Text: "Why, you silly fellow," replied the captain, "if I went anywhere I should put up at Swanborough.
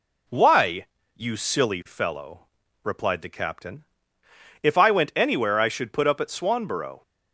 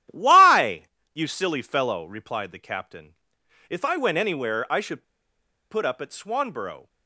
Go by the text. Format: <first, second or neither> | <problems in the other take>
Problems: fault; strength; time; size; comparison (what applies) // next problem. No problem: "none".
first | starts louder than the rest; strong; until 1.3 s; 11.5 dB // pauses between "should" and "put"; noticeable; at 5.0 s; 0.68 s long